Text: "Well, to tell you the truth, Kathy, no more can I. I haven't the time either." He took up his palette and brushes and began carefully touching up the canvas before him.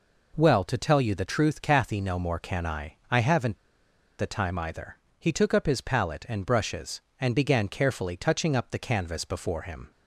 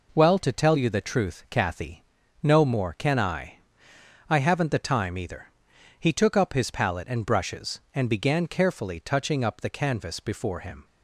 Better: second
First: pauses between "haven't" and "the"; noticeable; at 3.5 s; 0.64 s long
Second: none

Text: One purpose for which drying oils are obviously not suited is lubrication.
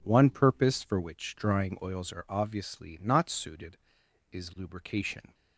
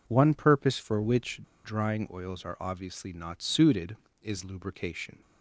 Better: first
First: none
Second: pauses between "which" and "drying"; slight; at 1.3 s; 0.24 s long

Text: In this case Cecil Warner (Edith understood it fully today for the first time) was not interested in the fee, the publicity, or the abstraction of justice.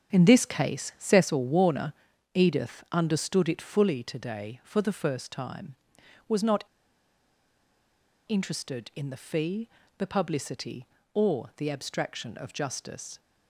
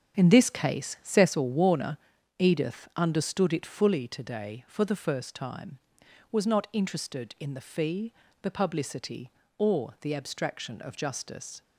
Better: second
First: starts louder than the rest; strong; until 1.2 s; 8 dB // pauses between "not" and "interested"; strong; at 6.6 s; 1.6 s long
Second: starts louder than the rest; strong; until 1.2 s; 8 dB

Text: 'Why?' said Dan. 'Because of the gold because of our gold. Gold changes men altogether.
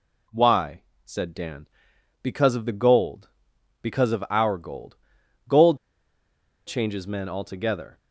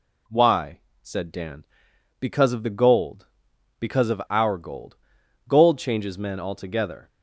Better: second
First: pauses between "Gold" and "changes"; noticeable; at 5.7 s; 0.89 s long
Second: none

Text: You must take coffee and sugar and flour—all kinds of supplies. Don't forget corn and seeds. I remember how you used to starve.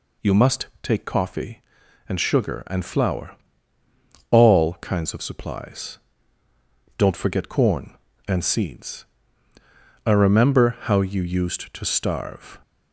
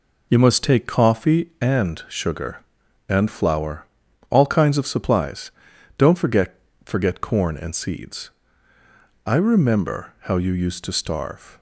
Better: first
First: none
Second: says "forget" twice; at 6.8 s

